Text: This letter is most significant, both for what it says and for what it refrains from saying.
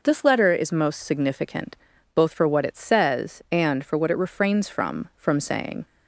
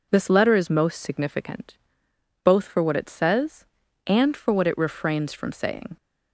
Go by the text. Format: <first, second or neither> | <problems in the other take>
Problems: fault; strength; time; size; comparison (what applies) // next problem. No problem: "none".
second | says "from" twice; at 5.1 s